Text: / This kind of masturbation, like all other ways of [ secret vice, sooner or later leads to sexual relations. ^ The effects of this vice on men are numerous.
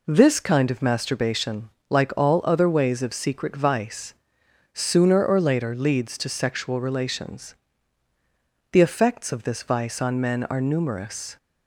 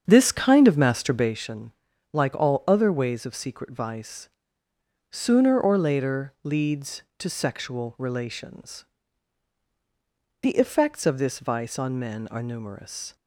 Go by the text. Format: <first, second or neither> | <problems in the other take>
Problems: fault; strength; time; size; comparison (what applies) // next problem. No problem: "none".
first | starts louder than the rest; strong; until 1.4 s; 7.5 dB